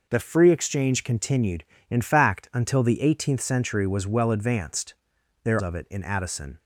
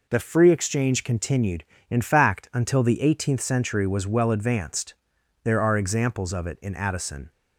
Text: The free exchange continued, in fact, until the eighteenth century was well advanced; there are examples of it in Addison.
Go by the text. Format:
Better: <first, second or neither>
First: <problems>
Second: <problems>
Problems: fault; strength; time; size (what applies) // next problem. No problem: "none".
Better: second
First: skips "are examples"; at 5.5 s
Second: none